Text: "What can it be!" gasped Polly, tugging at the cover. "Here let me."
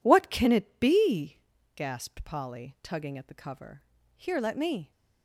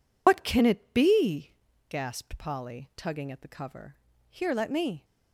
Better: first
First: none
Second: loses the start of "What"; at 0.2 s; 105 ms

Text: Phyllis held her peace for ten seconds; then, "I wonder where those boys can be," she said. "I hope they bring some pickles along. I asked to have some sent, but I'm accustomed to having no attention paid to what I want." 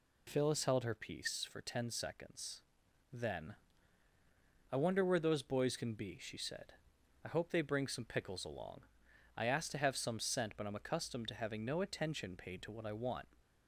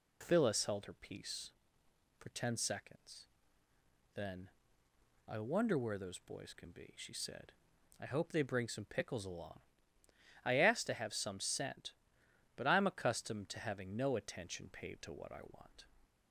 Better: neither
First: none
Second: none

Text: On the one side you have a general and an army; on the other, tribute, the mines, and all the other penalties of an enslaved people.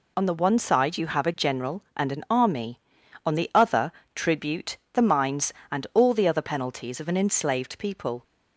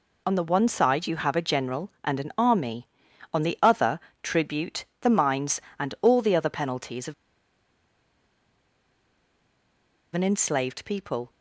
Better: first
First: none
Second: pauses between "of" and "an"; strong; at 7.1 s; 3.0 s long

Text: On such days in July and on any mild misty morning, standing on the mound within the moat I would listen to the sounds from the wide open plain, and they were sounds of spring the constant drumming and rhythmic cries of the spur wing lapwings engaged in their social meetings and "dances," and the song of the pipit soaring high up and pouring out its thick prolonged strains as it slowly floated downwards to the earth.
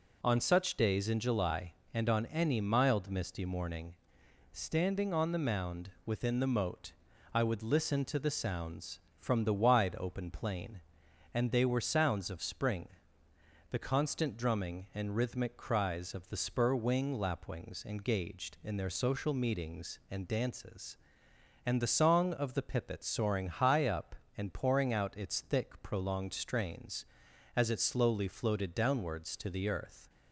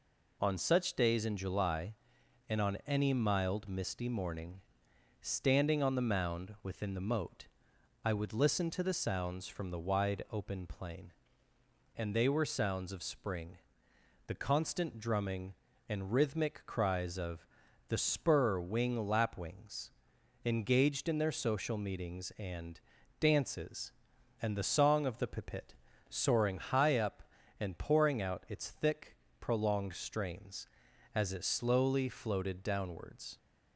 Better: first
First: pauses between "moat" and "I"; at 6.9 s; 0.42 s long // pauses between "spring" and "the"; noticeable; at 12.8 s; 0.80 s long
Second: pauses between "moat" and "I"; noticeable; at 7.4 s; 0.56 s long // pauses between "spring" and "the"; noticeable; at 13.5 s; 0.70 s long // pauses between "of" and "the"; at 17.4 s; 0.42 s long // pauses between "lapwings" and "engaged"; noticeable; at 19.9 s; 0.52 s long // pauses between "and" and "dances"; at 22.8 s; 0.40 s long // pauses between "pipit" and "soaring"; slight; at 25.7 s; 0.34 s long // pauses between "thick" and "prolonged"; slight; at 29.1 s; 0.26 s long // stops before "to the earth"; at 33.3 s

